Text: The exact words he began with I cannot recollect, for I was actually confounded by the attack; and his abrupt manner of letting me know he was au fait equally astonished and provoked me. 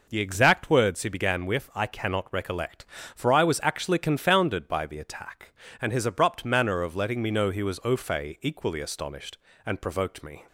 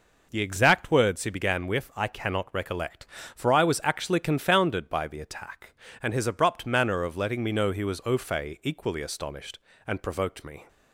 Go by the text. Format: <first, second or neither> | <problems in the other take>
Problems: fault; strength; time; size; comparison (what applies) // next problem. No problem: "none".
neither | none